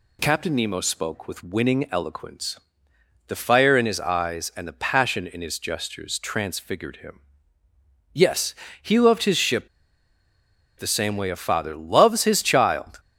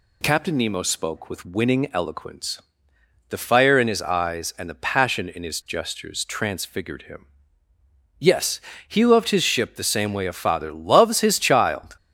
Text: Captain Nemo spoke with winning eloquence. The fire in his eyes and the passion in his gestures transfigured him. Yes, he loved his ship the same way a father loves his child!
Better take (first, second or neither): second